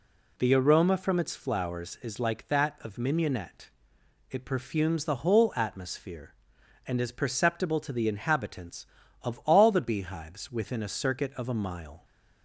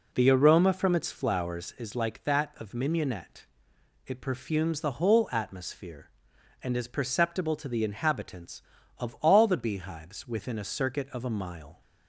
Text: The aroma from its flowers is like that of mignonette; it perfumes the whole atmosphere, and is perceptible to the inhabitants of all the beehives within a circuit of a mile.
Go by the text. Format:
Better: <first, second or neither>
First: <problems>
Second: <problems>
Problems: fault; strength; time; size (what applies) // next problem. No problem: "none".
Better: first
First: none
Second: starts louder than the rest; until 1.9 s; 4 dB